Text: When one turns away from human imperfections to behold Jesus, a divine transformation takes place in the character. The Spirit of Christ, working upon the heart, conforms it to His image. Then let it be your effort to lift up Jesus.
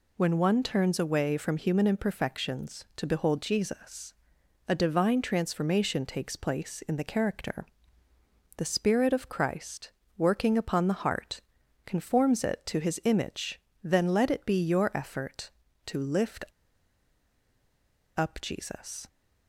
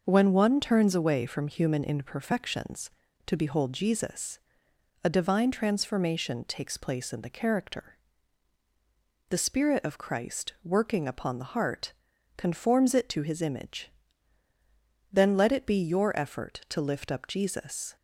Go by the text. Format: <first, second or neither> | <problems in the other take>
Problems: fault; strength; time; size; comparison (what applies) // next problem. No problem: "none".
second | pauses between "lift" and "up"; strong; at 16.4 s; 1.7 s long